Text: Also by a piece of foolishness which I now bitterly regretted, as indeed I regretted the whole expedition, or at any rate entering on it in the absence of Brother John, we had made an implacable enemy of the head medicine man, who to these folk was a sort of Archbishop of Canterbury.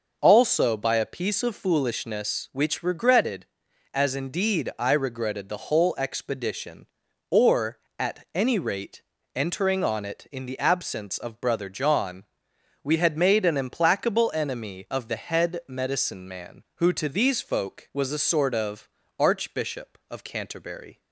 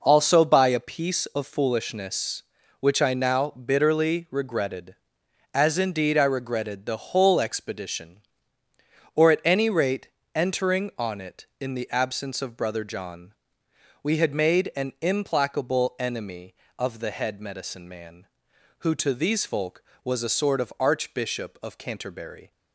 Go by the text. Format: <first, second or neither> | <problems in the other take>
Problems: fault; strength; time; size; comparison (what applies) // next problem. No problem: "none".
second | skips "I now bitterly"; at 2.8 s // pauses between "rate" and "entering"; slight; at 9.0 s; 0.32 s long; slight in the second // pauses between "of" and "Archbishop"; slight; at 18.8 s; 0.30 s long